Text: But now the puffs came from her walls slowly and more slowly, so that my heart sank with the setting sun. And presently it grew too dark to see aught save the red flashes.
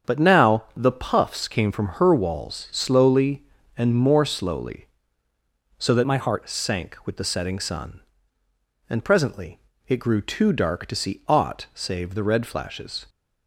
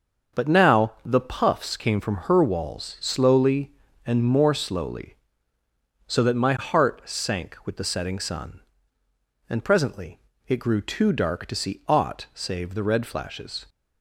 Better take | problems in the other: second | starts louder than the rest; strong; until 1.1 s; 7 dB; also in the second // changes voice from "my" to "heart"; from 6.0 to 6.4 s; 0.4 s long // pauses between "presently" and "it"; slight; at 9.5 s; 0.28 s long; slight in the second

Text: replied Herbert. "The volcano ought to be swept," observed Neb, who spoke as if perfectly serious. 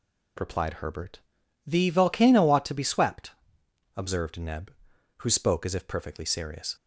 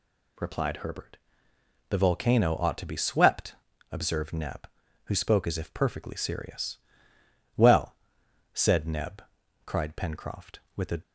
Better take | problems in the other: first | goes on to say "Well said Neb cried Pencroft with a"; strong; from 7.5 s on; 3.4 s long

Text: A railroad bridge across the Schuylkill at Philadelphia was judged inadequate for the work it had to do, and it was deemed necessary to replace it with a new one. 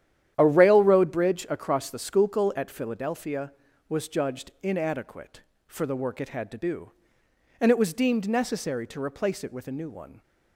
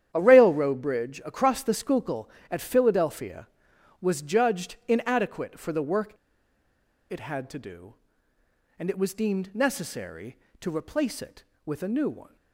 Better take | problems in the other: first | starts louder than the rest; strong; until 1.1 s; 10 dB; strong in the first // pauses between "work" and "it"; noticeable; at 6.1 s; 0.97 s long

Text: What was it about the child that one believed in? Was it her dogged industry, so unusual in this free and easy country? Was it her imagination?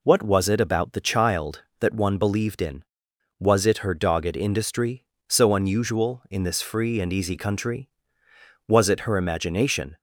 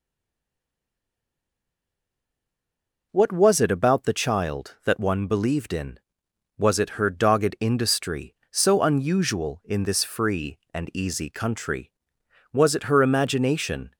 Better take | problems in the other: first | stays silent before the first word; strong; until 3.1 s; 3.1 s long

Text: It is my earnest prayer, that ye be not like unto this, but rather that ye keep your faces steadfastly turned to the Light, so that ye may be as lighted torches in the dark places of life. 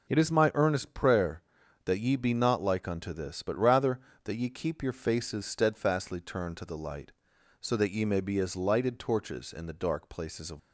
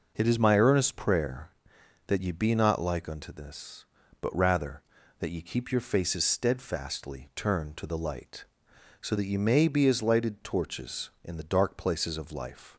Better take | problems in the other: second | stops before "life"; at 10.5 s

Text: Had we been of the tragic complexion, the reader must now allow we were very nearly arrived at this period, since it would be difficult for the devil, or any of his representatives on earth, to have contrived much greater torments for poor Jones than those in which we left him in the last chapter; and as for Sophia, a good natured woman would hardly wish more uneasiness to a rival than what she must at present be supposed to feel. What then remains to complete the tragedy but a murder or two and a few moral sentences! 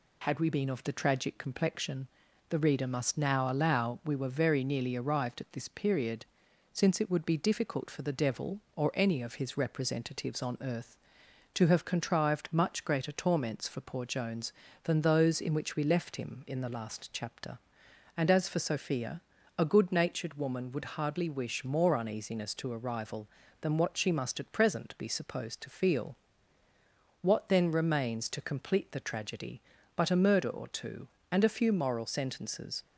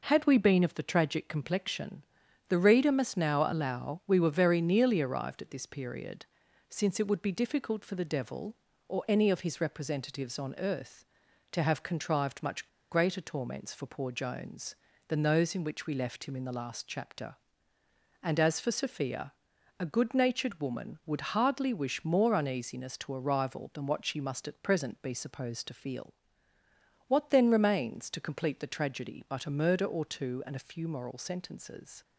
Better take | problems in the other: first | pauses between "much" and "greater"; slight; at 12.6 s; 0.23 s long

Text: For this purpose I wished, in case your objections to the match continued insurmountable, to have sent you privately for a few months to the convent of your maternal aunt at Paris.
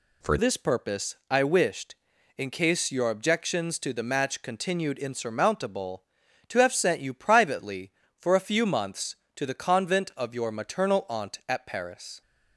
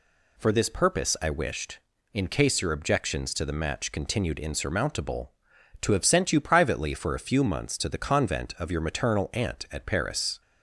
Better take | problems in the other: second | changes voice at "this"; from 0.3 s on; 11.9 s long

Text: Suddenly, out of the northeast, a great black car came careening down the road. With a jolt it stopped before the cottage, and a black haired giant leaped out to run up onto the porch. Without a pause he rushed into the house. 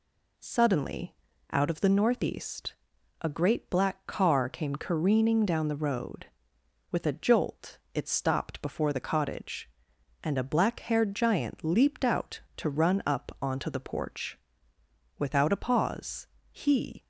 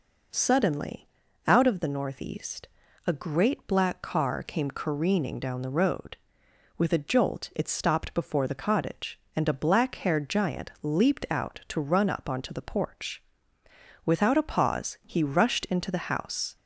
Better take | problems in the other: second | pauses between "jolt" and "it"; slight; at 7.7 s; 0.16 s long // pauses between "pause" and "he"; slight; at 16.2 s; 0.26 s long // stops before "rushed into the house"; at 17.0 s

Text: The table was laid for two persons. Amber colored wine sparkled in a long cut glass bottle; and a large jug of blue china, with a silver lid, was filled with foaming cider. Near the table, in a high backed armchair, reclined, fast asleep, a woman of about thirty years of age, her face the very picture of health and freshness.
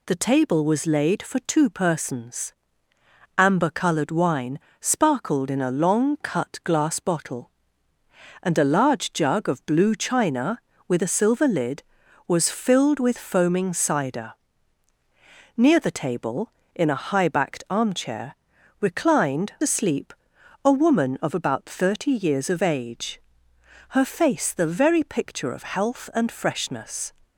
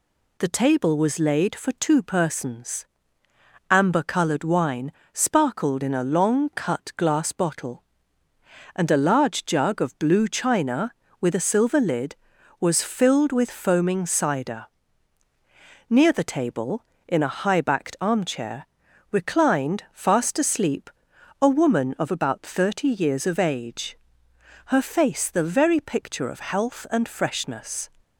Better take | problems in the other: second | pauses between "wine" and "sparkled"; slight; at 4.5 s; 0.22 s long; slight in the second // skips "fast"; at 19.5 s

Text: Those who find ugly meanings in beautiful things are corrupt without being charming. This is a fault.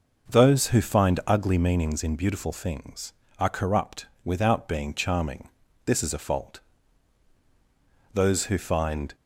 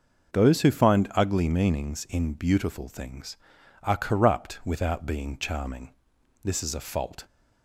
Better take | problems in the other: second | pauses between "corrupt" and "without"; slight; at 4.0 s; 0.18 s long // goes on to say "Those who find"; noticeable; from 8.1 s on; 1.0 s long

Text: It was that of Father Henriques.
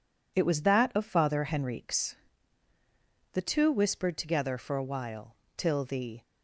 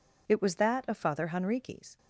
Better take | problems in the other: second | goes on to say "The two whispered together for a while till the"; strong; from 3.3 s on; 2.8 s long

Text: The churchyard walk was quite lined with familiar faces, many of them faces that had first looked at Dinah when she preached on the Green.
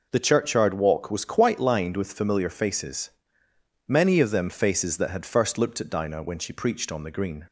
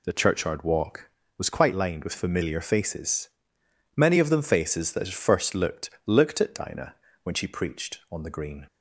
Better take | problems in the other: first | says "looked" twice; at 6.0 s // pauses between "Dinah" and "when"; slight; at 6.9 s; 0.30 s long

